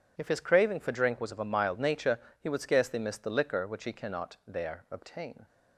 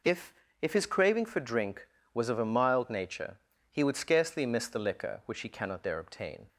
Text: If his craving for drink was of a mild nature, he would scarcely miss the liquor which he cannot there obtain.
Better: first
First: none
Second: says "If" twice; at 0.6 s

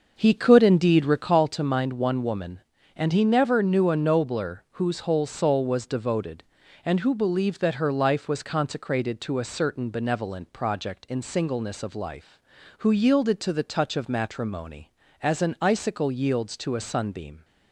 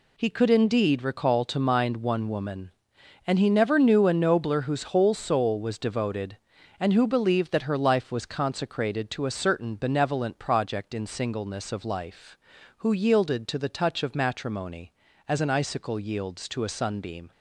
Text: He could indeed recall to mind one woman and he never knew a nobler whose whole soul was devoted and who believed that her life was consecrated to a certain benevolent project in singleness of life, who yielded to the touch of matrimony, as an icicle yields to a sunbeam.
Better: second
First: starts louder than the rest; until 1.4 s; 6.5 dB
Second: none

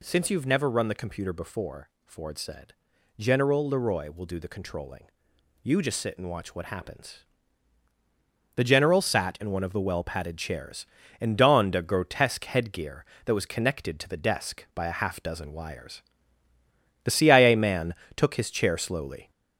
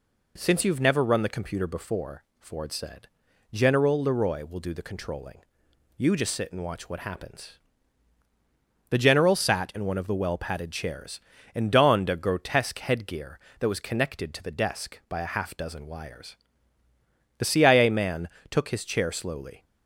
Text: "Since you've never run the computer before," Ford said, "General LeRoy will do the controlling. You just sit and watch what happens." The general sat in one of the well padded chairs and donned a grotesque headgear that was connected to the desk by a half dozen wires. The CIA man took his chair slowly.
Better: second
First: gets louder; noticeable; throughout; 4 dB // pauses between "man" and "took"; slight; at 17.9 s; 0.22 s long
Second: pauses between "man" and "took"; slight; at 18.2 s; 0.22 s long

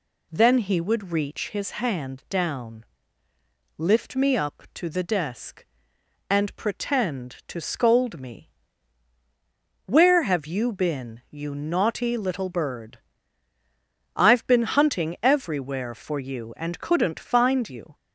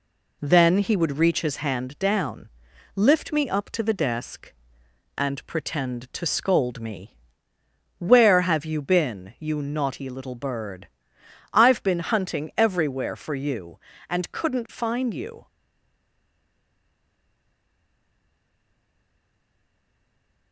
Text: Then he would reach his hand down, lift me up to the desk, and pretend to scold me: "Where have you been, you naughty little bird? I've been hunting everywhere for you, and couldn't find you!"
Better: first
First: none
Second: stays silent after the last word; strong; from 15.4 s on; 5.1 s long

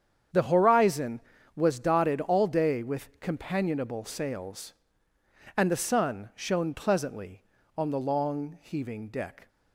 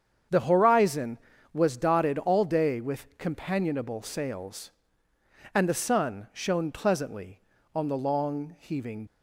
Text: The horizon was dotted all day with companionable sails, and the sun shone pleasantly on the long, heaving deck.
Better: first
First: starts louder than the rest; strong; until 1.6 s; 8 dB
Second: starts louder than the rest; strong; until 1.6 s; 8 dB // stops before "deck"; at 9.0 s

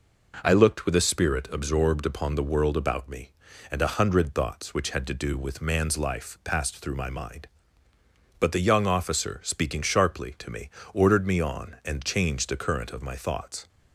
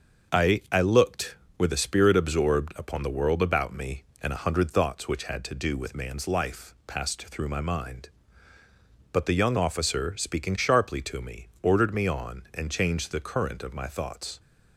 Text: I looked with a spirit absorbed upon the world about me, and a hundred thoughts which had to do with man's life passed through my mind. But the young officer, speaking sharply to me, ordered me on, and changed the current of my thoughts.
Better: first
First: none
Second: starts louder than the rest; until 1.6 s; 6.5 dB // says "I" twice; at 0.7 s

